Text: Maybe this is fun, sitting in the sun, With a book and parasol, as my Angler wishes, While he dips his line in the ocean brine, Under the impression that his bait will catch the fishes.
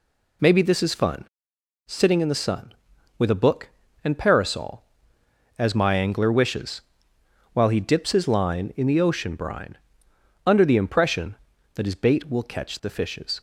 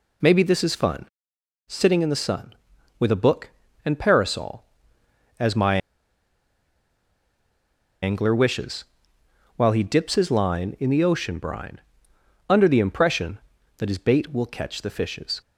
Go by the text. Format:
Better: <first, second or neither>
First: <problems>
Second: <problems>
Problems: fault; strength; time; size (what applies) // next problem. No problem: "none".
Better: first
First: none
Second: pauses between "my" and "Angler"; strong; at 5.7 s; 2.2 s long